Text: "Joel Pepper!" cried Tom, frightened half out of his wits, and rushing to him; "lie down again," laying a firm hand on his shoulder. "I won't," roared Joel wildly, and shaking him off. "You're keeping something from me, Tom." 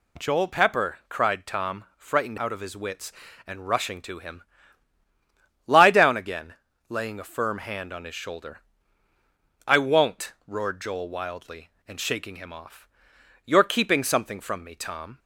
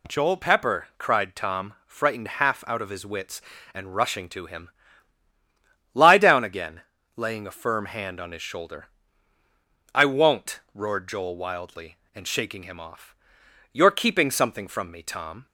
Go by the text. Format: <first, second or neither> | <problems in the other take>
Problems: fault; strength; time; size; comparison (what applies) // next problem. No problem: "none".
second | skips "half"; at 2.3 s